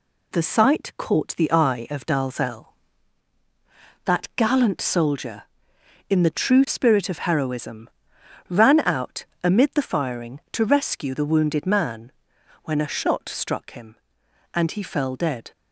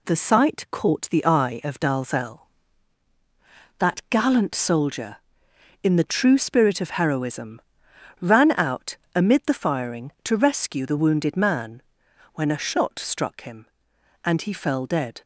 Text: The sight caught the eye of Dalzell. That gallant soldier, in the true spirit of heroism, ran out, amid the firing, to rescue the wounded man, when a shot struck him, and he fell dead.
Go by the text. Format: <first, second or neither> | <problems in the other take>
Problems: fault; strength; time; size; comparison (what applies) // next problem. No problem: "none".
neither | none